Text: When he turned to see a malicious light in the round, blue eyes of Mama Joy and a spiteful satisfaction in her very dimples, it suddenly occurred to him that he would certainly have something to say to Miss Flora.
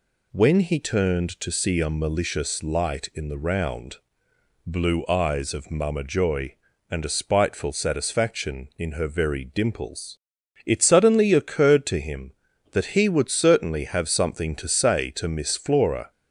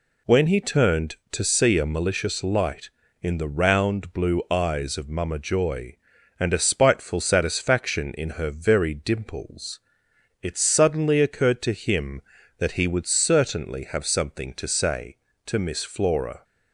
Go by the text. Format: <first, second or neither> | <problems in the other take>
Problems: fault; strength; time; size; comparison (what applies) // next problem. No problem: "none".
neither | none